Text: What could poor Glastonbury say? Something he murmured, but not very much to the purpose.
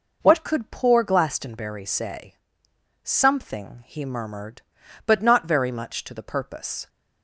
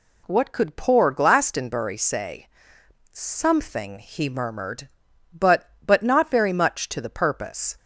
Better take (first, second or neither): first